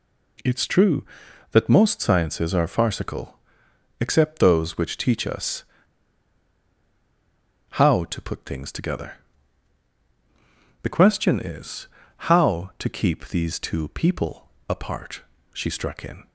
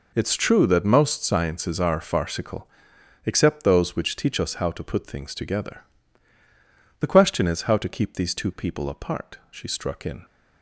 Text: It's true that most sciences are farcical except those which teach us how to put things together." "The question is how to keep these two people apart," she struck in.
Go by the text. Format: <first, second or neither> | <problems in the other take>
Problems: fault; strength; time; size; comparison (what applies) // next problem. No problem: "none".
second | pauses between "farcical" and "except"; noticeable; at 3.3 s; 0.66 s long; noticeable in the second // pauses between "us" and "how"; strong; at 5.6 s; 2.0 s long // pauses between "is" and "how"; at 11.8 s; 0.40 s long // pauses between "people" and "apart"; slight; at 14.4 s; 0.18 s long